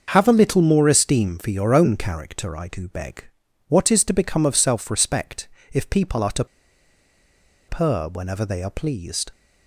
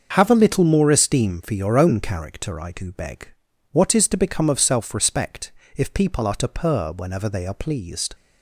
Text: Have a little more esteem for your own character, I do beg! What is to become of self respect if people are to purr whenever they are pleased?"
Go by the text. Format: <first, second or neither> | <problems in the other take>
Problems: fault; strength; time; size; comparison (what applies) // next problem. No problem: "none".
second | starts louder than the rest; until 1.1 s; 6.5 dB; also in the second // pauses between "respect" and "if"; slight; at 5.4 s; 0.24 s long; slight in the second // pauses between "to" and "purr"; at 6.4 s; 1.2 s long